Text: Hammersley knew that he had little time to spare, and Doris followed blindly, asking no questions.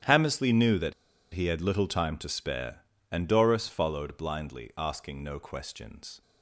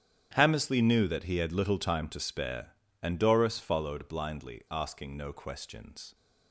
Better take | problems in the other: second | starts louder than the rest; strong; until 1.4 s; 9.5 dB; strong in the second // pauses between "that" and "he"; at 0.9 s; 0.39 s long

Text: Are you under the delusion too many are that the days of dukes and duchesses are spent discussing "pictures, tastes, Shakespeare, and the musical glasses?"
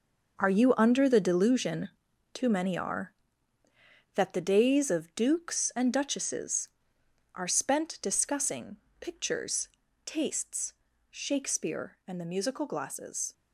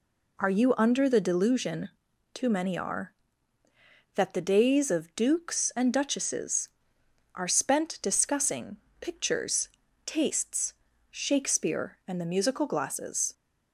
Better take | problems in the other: second | gets quieter; strong; throughout; 10.5 dB // pauses between "delusion" and "too"; noticeable; at 1.8 s; 0.46 s long; noticeable in the second // pauses between "discussing" and "pictures"; slight; at 8.7 s; 0.24 s long; slight in the second

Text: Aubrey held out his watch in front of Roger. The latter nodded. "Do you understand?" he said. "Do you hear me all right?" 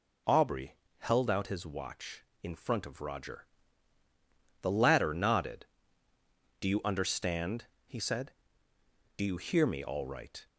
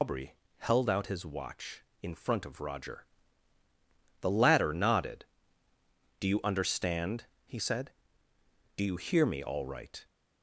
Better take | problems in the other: first | loses the start of "Aubrey"; at 0.0 s; 155 ms // pauses between "Aubrey" and "held"; slight; at 0.3 s; 0.22 s long; slight in the first

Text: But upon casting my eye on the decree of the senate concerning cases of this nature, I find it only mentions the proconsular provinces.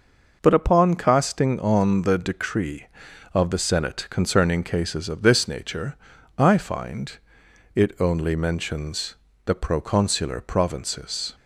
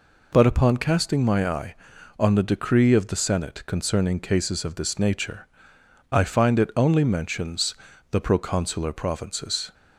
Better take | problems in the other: second | skips "my eye"; at 1.5 s // pauses between "find" and "it"; noticeable; at 7.1 s; 0.58 s long // pauses between "mentions" and "the"; slight; at 9.1 s; 0.30 s long; slight in the second

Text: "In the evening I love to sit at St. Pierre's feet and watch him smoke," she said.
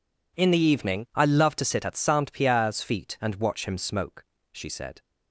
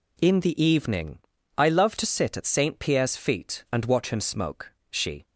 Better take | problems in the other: first | pauses between "evening" and "I"; at 1.1 s; 0.40 s long // stops before "said"; at 5.2 s

